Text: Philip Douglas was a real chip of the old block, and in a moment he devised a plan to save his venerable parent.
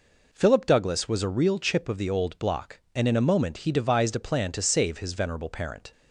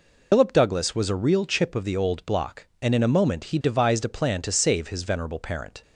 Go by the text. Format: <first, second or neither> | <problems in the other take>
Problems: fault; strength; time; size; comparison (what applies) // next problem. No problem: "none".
first | loses the start of "Philip"; at 0.3 s; 130 ms